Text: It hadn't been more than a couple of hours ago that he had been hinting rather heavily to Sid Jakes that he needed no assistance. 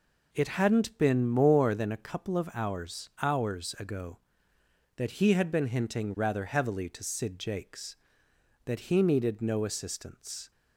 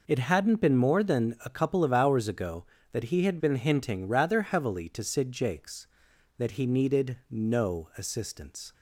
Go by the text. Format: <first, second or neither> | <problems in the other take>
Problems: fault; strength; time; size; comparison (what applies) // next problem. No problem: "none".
second | says "hours" twice; at 3.2 s